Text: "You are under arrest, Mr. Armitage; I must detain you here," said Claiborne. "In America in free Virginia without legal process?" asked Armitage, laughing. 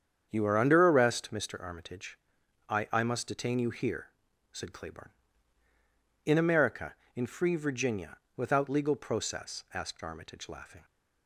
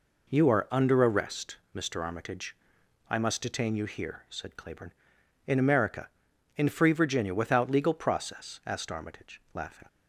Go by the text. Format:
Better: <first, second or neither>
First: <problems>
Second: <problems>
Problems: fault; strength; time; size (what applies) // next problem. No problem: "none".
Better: second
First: starts louder than the rest; strong; until 1.3 s; 8 dB // says "I" twice; at 2.9 s // pauses between "Virginia" and "without"; slight; at 8.1 s; 0.18 s long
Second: none